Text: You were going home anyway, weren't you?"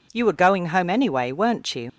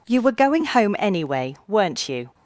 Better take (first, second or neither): second